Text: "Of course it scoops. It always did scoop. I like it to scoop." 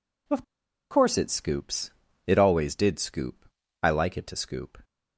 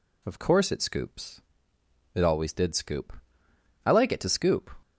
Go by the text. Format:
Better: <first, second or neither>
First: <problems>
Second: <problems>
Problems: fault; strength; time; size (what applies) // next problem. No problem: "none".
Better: second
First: pauses between "Of" and "course"; noticeable; at 0.4 s; 0.48 s long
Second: none